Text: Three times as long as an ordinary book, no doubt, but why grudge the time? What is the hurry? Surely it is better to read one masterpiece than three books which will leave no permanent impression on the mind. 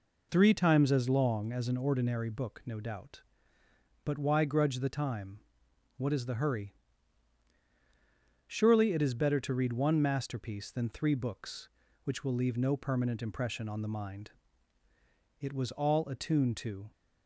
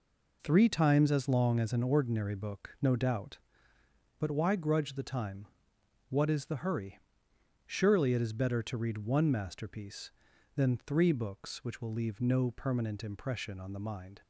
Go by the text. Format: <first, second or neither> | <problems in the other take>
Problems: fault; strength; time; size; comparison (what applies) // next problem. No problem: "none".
second | goes on to say "It was all attuned to"; from 15.3 s on; 1.5 s long